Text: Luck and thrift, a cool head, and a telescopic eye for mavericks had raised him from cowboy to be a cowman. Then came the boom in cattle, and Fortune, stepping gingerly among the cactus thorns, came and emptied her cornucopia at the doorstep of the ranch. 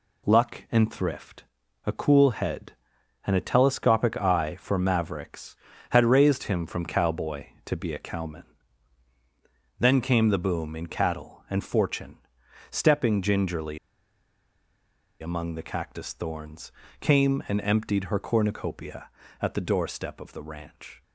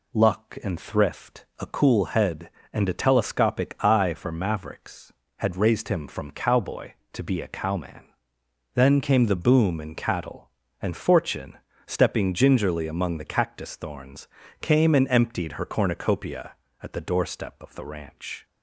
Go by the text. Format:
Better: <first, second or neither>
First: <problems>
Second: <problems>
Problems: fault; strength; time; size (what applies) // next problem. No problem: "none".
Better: second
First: pauses between "gingerly" and "among"; strong; at 13.7 s; 1.4 s long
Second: none